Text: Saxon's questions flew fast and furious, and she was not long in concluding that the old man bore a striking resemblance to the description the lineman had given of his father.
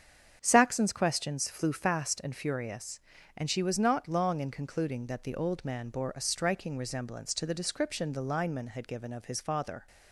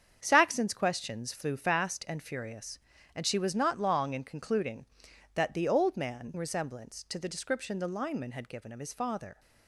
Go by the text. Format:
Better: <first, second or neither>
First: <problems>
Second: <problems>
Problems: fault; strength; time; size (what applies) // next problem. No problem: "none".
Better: first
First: starts louder than the rest; strong; until 1.4 s; 7.5 dB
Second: starts louder than the rest; strong; until 1.2 s; 7.5 dB // skips "bore a striking"; at 6.3 s